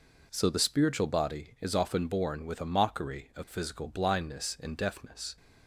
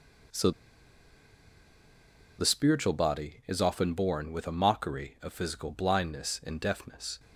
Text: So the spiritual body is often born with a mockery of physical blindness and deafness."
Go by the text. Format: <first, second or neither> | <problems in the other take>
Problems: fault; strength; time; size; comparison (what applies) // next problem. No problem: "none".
first | pauses between "So" and "the"; strong; at 0.5 s; 1.8 s long